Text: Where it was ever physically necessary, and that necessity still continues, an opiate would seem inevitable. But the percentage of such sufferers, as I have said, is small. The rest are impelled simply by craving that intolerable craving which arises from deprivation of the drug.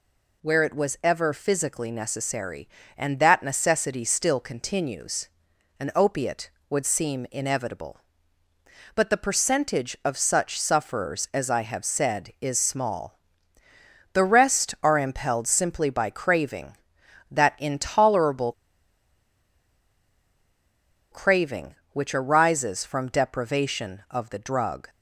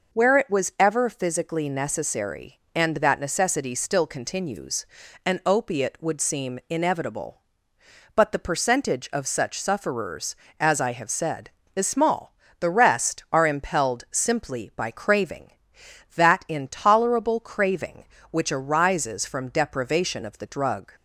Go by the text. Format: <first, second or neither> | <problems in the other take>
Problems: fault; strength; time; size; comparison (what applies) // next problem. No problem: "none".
second | pauses between "intolerable" and "craving"; strong; at 18.5 s; 2.5 s long